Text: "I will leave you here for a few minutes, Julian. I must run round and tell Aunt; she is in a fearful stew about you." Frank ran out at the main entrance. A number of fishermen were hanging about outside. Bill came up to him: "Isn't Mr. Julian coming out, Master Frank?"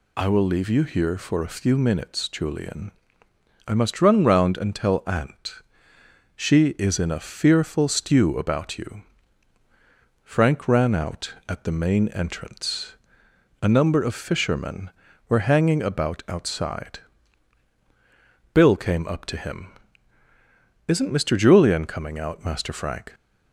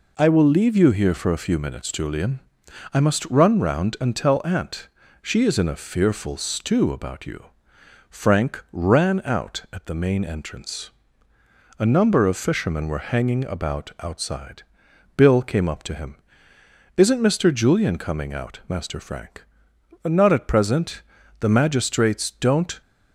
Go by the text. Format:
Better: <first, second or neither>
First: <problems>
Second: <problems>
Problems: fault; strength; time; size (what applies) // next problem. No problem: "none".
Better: first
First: none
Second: goes on to say "Not at present The magistrates don't"; strong; from 20.0 s on; 2.7 s long